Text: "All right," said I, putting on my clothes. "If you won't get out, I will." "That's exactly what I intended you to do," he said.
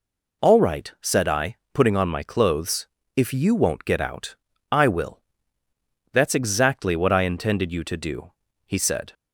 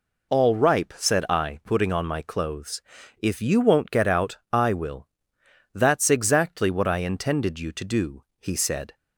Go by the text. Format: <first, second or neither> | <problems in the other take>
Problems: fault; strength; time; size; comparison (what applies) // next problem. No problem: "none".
first | says "ripe" for "right"; at 0.5 s